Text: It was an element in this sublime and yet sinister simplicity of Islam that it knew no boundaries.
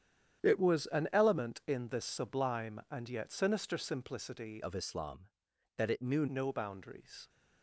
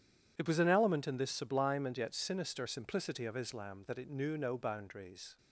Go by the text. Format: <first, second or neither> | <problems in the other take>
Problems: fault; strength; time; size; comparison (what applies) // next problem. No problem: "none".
second | starts louder than the rest; strong; until 1.4 s; 9.5 dB // changes voice from "of" to "knew"; from 4.6 to 6.2 s; 1.6 s long